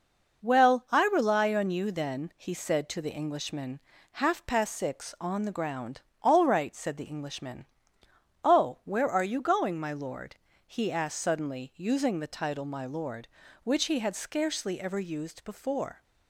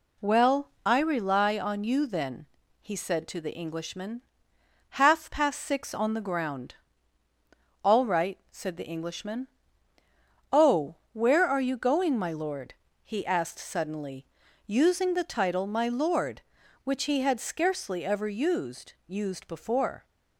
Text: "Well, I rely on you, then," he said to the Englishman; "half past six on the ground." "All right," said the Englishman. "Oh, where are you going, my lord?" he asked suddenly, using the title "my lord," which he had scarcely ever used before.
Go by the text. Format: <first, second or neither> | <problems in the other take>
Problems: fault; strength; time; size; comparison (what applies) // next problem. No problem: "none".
first | says "used" twice; at 19.0 s